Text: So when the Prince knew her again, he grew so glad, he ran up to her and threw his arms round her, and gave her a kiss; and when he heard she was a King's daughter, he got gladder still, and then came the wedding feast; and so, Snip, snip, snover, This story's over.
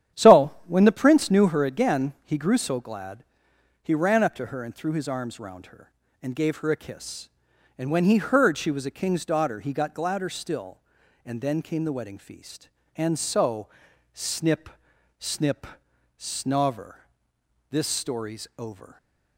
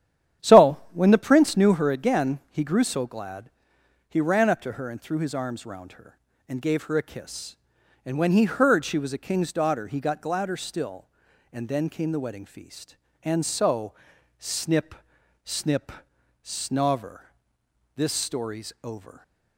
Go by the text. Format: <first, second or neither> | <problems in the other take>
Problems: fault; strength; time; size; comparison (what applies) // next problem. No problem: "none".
neither | starts louder than the rest; strong; the same in both